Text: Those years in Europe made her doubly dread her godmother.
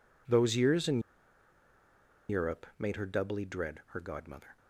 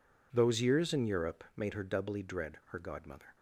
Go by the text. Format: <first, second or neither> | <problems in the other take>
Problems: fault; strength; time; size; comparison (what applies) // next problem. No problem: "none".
second | pauses between "in" and "Europe"; strong; at 1.0 s; 1.2 s long